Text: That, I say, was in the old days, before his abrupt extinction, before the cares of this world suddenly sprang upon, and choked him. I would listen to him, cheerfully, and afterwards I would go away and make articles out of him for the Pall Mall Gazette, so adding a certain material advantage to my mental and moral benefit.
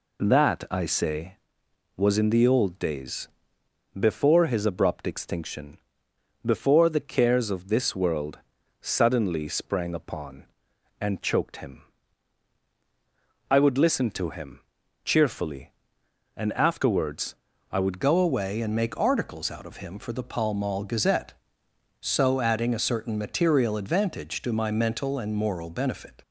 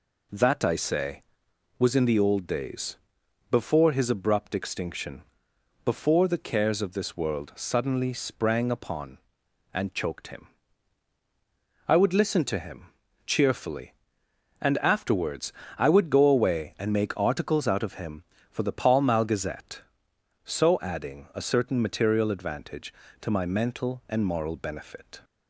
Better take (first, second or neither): second